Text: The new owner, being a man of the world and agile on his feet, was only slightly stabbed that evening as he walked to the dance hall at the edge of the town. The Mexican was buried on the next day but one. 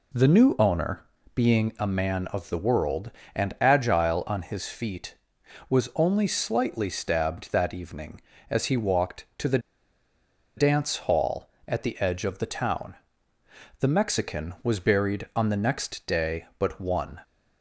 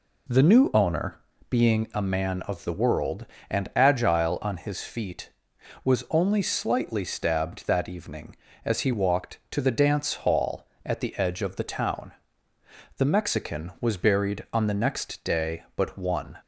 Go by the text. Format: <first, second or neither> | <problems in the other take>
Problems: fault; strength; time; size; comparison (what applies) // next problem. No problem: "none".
second | pauses between "the" and "dance"; at 9.5 s; 0.98 s long